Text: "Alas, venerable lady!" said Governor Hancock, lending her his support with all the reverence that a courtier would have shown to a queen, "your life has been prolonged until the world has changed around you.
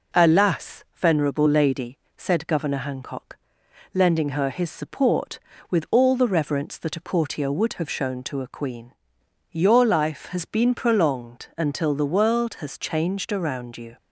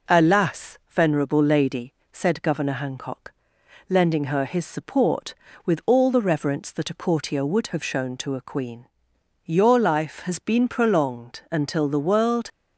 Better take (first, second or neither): first